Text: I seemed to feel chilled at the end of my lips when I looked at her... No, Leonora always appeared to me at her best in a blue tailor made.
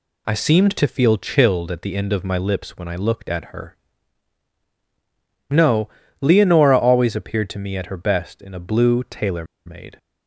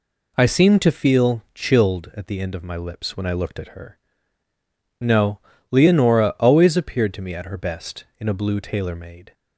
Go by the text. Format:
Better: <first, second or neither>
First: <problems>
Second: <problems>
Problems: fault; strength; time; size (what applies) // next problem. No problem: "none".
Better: second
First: pauses between "tailor" and "made"; slight; at 9.4 s; 0.20 s long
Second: none